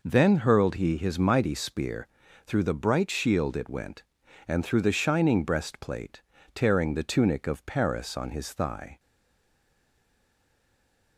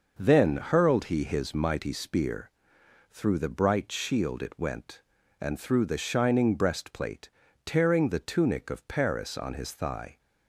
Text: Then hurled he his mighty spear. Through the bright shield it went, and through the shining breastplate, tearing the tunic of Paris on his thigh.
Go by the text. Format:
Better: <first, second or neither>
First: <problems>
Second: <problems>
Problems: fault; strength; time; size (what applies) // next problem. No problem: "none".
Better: second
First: stays silent after the last word; from 8.9 s on; 2.2 s long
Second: none